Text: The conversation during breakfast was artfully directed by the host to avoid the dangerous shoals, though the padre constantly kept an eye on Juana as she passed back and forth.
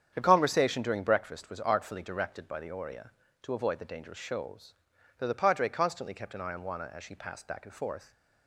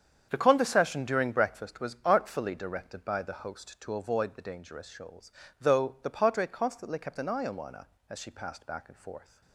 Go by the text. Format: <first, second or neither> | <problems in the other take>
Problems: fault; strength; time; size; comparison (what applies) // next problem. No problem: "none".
second | starts louder than the rest; strong; until 1.1 s; 8.5 dB; strong in the second // says "oria" for "host"; at 2.7 s